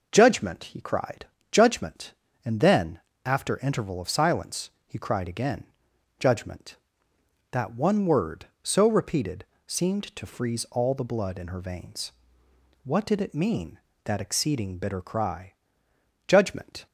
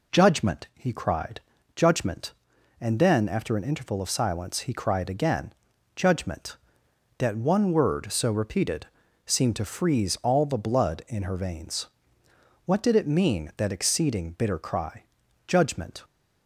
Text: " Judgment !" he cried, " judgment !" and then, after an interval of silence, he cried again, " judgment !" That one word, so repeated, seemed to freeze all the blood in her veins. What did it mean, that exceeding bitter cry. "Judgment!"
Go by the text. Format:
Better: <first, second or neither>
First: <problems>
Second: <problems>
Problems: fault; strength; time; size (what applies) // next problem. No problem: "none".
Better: second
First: skips "an"; at 3.5 s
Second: none